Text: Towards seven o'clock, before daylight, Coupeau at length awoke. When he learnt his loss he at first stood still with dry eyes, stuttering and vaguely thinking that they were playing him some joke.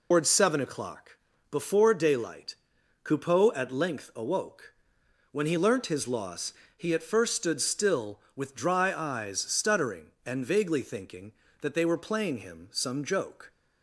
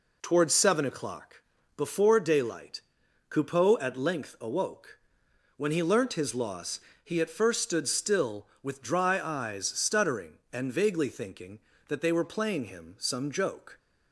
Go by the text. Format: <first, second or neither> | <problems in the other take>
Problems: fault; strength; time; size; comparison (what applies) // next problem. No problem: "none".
second | loses the start of "Towards"; at 0.1 s; 130 ms // pauses between "loss" and "he"; slight; at 6.5 s; 0.24 s long; slight in the second